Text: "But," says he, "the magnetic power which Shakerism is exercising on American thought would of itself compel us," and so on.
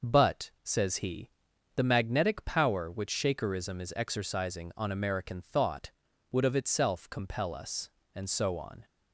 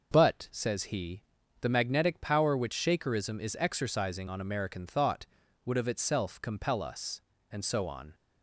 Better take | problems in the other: neither | none

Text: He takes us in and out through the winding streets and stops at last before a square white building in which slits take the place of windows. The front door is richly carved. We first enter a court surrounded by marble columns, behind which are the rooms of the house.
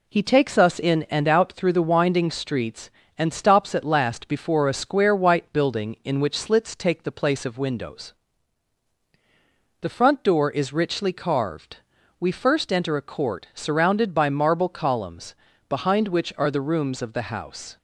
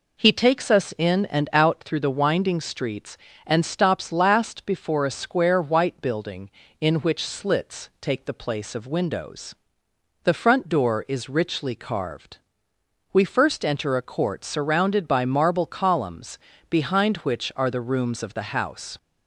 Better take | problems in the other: first | skips "at"; at 4.1 s

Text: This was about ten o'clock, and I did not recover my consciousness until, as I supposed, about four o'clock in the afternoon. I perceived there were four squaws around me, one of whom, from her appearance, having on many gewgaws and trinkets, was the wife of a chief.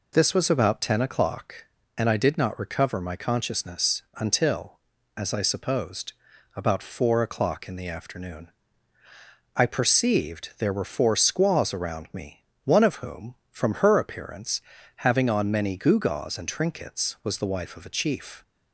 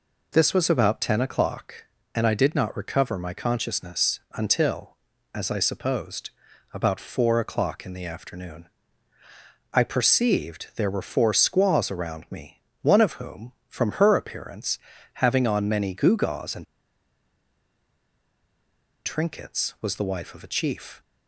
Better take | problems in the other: first | pauses between "consciousness" and "until"; slight; at 4.1 s; 0.16 s long; slight in the first // pauses between "and" and "trinkets"; strong; at 16.6 s; 2.4 s long

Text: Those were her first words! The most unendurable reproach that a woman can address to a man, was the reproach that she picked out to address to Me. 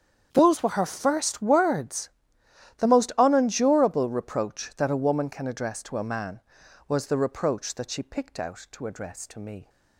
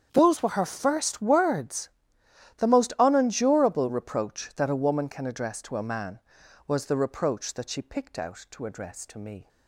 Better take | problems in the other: neither | starts louder than the rest; strong; the same in both

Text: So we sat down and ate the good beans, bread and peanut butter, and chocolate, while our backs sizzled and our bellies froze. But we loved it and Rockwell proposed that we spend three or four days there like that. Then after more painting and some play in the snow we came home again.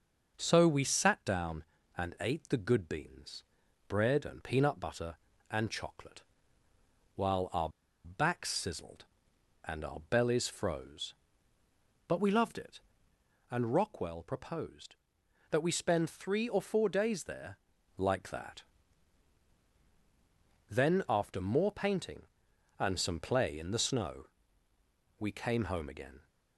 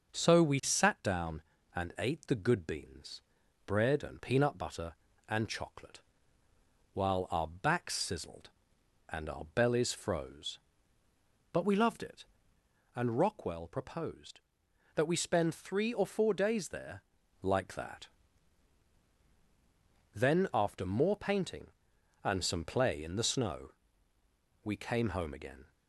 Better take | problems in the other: second | pauses between "our" and "backs"; at 7.6 s; 0.36 s long // pauses between "there" and "like"; at 17.5 s; 0.40 s long; also in the second // pauses between "snow" and "we"; noticeable; at 24.2 s; 0.92 s long; noticeable in the second

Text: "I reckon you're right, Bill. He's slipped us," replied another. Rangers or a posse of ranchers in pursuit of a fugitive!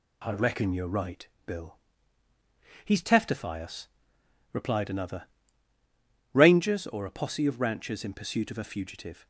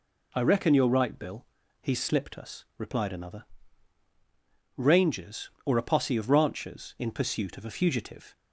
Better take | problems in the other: second | says "teftify" for "slipped"; at 3.0 s

